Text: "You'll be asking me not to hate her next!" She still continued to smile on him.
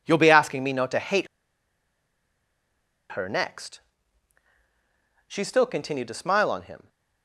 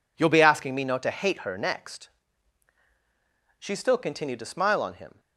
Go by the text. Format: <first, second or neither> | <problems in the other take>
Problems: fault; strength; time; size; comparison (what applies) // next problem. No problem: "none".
second | pauses between "hate" and "her"; strong; at 1.2 s; 1.8 s long